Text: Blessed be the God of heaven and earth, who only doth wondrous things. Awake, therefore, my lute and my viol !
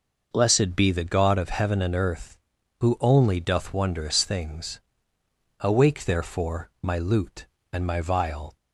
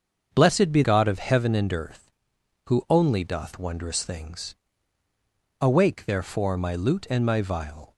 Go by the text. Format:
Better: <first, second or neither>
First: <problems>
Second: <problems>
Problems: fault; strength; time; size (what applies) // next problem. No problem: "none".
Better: first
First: none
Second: starts louder than the rest; until 1.3 s; 7 dB // skips "the"; at 0.8 s